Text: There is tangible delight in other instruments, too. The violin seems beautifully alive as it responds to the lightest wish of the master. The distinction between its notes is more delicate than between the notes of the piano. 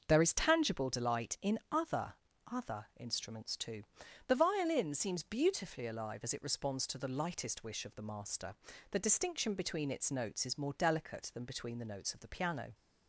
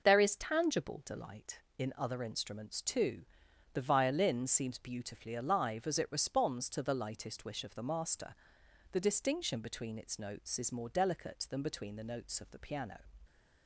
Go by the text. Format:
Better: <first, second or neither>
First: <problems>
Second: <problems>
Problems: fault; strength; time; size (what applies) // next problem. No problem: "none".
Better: second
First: starts louder than the rest; until 1.0 s; 6 dB // says "other" twice; at 2.5 s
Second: none